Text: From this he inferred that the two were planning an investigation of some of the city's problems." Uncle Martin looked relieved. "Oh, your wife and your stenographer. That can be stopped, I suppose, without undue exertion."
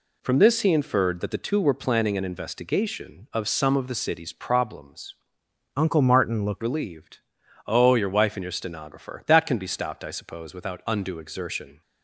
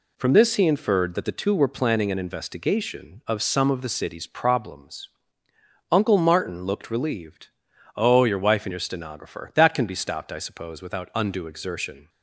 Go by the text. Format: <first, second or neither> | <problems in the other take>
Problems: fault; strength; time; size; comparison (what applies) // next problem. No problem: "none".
second | changes voice from "Uncle" to "looked"; from 5.7 to 6.6 s; 0.9 s long